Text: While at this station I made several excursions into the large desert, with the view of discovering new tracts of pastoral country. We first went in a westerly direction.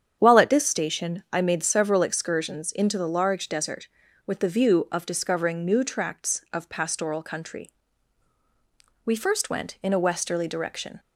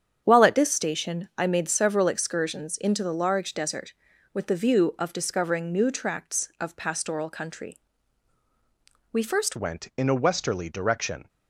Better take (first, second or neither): first